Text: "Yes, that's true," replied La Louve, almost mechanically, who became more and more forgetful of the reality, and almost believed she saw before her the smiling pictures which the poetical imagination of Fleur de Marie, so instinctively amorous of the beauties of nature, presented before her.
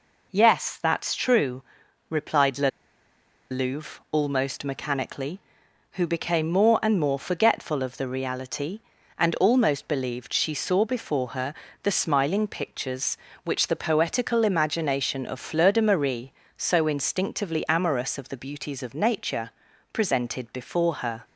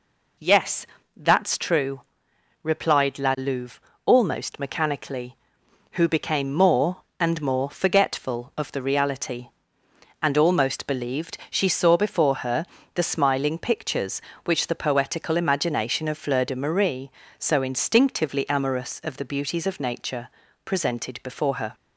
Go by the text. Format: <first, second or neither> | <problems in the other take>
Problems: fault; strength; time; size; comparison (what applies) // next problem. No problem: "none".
second | pauses between "La" and "Louve"; noticeable; at 2.6 s; 0.81 s long // pauses between "her" and "the"; slight; at 11.5 s; 0.26 s long; slight in the second